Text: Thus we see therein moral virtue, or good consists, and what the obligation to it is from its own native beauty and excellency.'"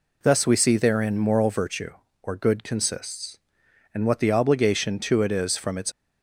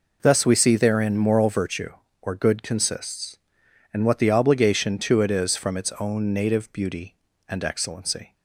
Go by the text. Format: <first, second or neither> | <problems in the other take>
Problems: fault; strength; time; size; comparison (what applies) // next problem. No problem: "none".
second | stops before "own native beauty and excellency"; at 5.9 s